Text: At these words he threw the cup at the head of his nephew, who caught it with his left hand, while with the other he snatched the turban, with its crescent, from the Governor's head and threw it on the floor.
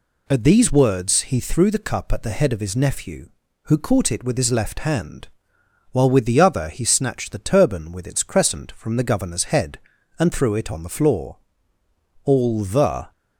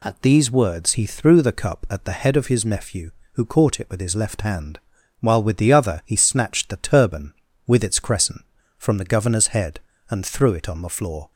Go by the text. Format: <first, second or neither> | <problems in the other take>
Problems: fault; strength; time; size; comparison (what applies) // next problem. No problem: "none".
second | goes on to say "All the"; noticeable; from 12.2 s on; 0.88 s long